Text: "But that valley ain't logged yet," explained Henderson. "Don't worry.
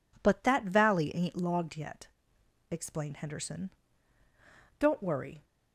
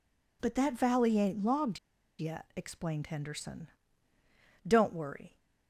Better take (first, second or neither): first